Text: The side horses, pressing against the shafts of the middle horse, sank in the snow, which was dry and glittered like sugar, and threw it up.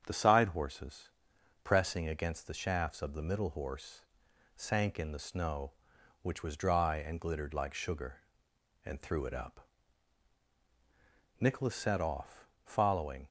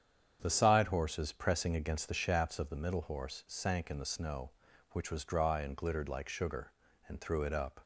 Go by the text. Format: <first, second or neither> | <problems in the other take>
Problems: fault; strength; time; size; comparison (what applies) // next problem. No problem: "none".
second | starts louder than the rest; strong; until 1.0 s; 7.5 dB; strong in the second // goes on to say "Nicholas set off following"; strong; from 11.3 s on; 1.8 s long